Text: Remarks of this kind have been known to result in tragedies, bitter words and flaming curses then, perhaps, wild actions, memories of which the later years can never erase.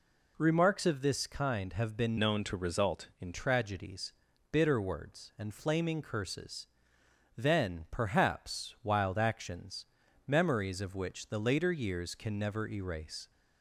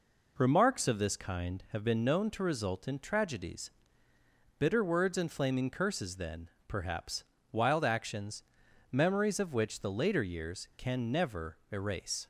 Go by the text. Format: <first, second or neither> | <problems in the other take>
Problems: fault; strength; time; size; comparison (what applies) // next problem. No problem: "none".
second | changes voice from "known" to "in"; from 2.1 to 3.3 s; 1.2 s long // pauses between "curses" and "then"; noticeable; at 6.6 s; 0.72 s long